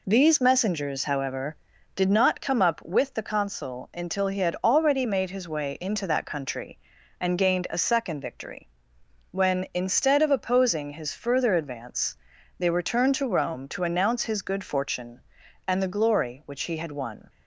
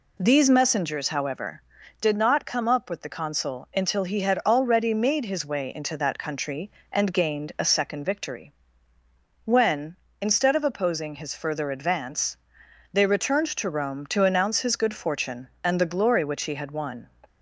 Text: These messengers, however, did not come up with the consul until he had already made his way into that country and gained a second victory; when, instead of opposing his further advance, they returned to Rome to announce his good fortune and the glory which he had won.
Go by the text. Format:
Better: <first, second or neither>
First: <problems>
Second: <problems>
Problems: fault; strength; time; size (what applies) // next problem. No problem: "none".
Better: neither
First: none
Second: none